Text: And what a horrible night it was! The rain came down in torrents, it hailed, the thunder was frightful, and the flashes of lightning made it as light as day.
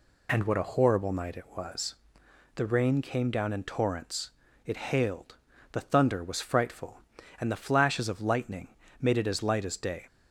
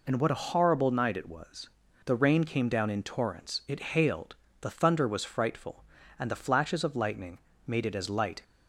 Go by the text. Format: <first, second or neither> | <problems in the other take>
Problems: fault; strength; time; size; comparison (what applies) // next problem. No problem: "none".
first | pauses between "lightning" and "made"; slight; at 7.3 s; 0.28 s long; slight in the first // stops before "as day"; at 8.4 s